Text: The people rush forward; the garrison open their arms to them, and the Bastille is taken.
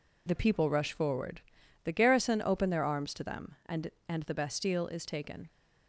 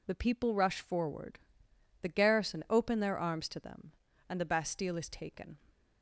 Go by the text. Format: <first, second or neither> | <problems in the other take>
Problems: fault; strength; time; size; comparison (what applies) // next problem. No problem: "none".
second | says "and" twice; at 4.0 s